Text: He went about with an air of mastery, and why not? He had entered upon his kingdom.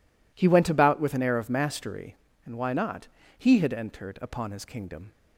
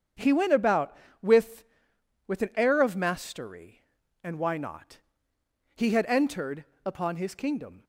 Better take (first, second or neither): first